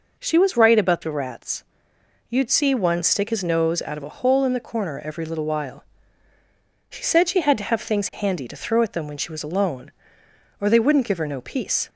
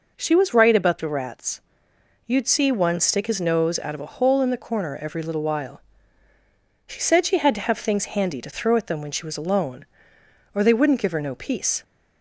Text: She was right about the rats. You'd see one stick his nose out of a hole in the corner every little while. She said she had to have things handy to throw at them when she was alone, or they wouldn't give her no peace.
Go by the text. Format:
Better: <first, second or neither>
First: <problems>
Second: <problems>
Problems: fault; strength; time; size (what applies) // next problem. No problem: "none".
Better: neither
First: none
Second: none